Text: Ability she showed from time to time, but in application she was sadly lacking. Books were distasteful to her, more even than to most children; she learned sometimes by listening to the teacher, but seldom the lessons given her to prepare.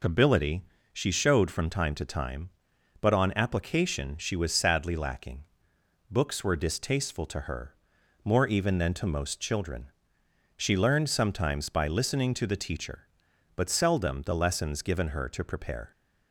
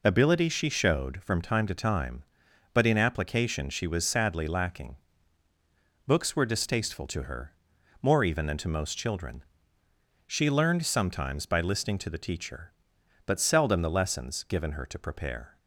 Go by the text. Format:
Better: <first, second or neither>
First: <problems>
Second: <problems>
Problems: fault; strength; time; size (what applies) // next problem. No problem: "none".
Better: second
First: pauses between "Ability" and "she"; slight; at 0.6 s; 0.28 s long // says "on" for "in"; at 3.1 s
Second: none